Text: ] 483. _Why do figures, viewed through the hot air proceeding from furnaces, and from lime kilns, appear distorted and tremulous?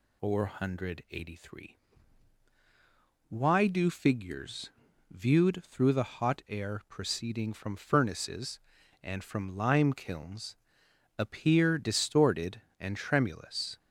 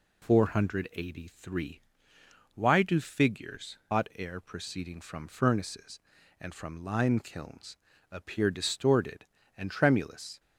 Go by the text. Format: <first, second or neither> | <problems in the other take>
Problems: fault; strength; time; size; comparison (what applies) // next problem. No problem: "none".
first | skips "viewed through the"; at 3.8 s